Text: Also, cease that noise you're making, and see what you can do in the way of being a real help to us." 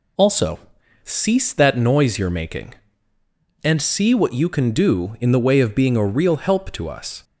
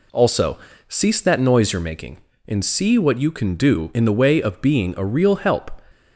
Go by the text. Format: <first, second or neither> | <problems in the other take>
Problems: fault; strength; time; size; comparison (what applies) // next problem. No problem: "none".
first | stops before "to us"; at 5.9 s